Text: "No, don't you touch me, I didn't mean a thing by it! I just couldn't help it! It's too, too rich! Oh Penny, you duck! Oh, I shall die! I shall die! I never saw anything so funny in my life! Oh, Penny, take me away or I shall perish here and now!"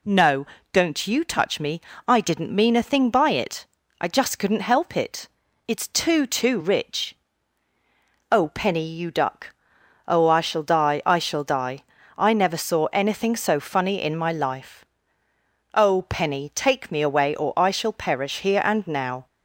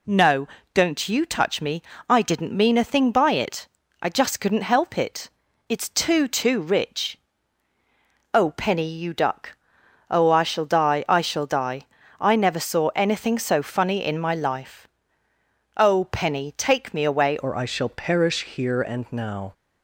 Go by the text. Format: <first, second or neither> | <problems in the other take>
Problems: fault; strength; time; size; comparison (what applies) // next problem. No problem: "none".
first | changes voice at "or"; from 17.3 s on; 2.2 s long